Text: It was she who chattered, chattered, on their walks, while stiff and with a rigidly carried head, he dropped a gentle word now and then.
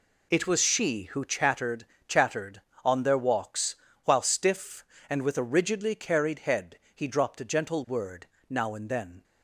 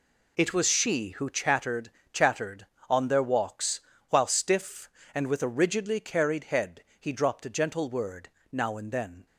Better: neither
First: pauses between "word" and "now"; slight; at 8.2 s; 0.22 s long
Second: pauses between "word" and "now"; slight; at 8.2 s; 0.22 s long

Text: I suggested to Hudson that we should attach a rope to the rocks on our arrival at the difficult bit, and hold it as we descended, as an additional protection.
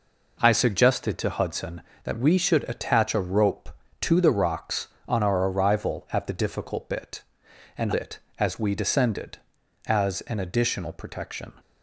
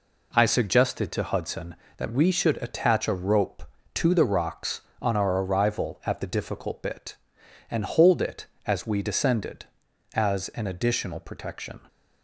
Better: second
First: skips "hold"; at 7.9 s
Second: none

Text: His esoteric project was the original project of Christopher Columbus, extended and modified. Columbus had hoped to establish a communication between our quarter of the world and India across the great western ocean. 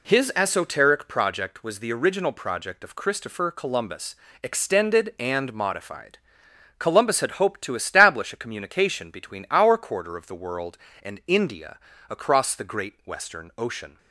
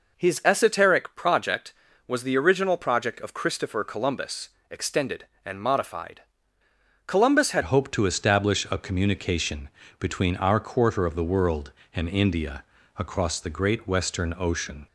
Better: first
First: pauses between "India" and "across"; slight; at 11.7 s; 0.28 s long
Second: changes voice at "hoped"; from 7.6 s on; 7.2 s long // pauses between "communication" and "between"; slight; at 9.6 s; 0.32 s long // pauses between "India" and "across"; slight; at 12.6 s; 0.34 s long

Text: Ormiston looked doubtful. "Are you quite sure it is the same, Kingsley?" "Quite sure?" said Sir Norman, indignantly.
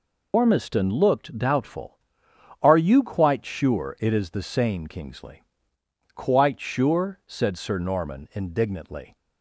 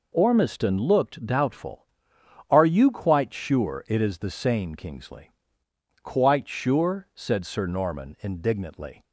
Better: second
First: loses the start of "Ormiston"; at 0.3 s; 90 ms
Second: none

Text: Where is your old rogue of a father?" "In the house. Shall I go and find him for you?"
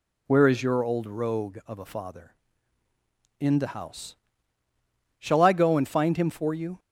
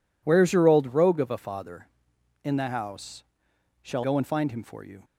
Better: first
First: none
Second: skips "I"; at 4.0 s

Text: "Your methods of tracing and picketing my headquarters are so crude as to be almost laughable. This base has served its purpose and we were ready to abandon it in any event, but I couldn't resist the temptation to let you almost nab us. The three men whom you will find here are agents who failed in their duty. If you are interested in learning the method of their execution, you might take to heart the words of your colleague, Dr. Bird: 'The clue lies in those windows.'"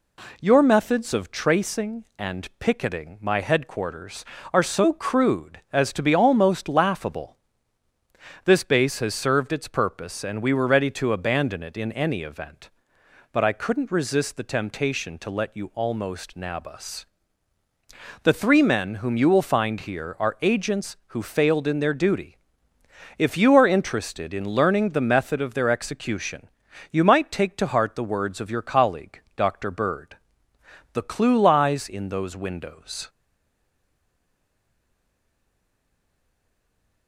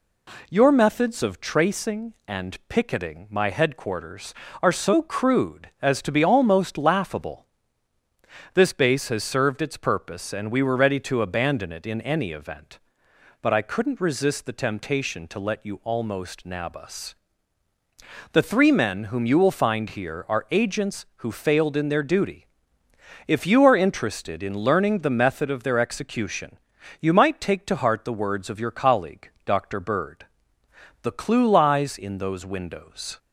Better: second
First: stays silent after the last word; strong; from 33.0 s on; 4.0 s long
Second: none

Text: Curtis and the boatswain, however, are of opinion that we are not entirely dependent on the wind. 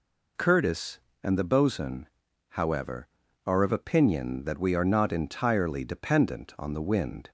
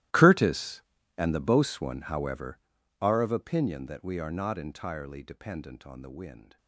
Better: first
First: none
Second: gets quieter; strong; throughout; 21 dB

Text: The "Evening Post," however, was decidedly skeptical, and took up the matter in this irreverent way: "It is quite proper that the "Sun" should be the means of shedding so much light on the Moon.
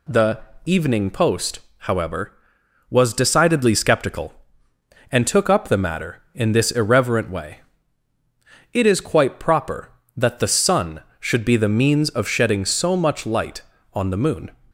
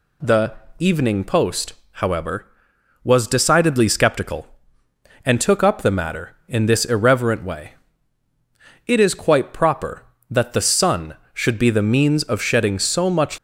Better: first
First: pauses between "The" and "Evening"; slight; at 0.3 s; 0.24 s long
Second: pauses between "The" and "Evening"; slight; at 0.5 s; 0.24 s long // stops before "light on the Moon"; at 13.3 s

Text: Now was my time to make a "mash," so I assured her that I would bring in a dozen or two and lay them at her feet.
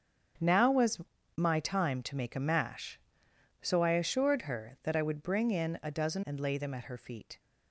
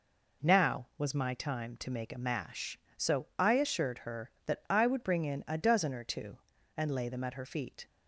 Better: second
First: starts louder than the rest; strong; until 1.7 s; 8 dB // pauses between "was" and "my"; slight; at 1.0 s; 0.36 s long // skips "or two"; at 6.2 s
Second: none

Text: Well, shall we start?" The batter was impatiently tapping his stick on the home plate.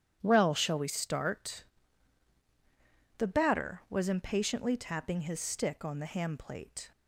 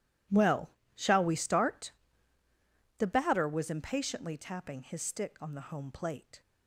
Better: second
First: starts louder than the rest; strong; until 1.2 s; 10 dB // says "ham" for "home"; at 6.0 s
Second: none

